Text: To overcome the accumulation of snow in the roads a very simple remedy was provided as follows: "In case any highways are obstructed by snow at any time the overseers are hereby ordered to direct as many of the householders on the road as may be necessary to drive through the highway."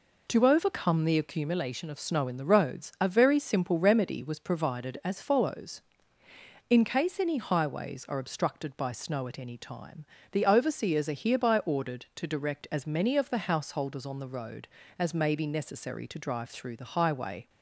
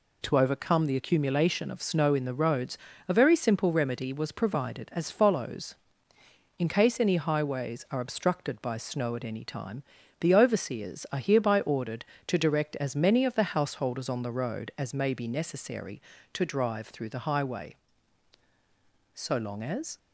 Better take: first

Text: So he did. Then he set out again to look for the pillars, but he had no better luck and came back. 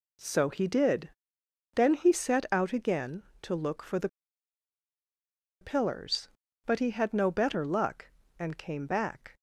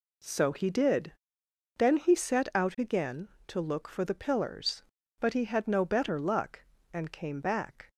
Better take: second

